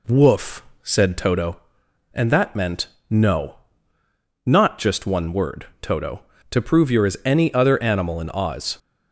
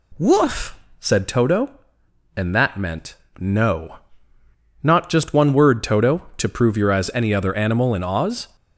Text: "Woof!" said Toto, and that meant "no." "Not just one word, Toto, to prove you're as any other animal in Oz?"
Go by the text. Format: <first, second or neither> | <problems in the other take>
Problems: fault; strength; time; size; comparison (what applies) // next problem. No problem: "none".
neither | pauses between "meant" and "no"; slight; the same in both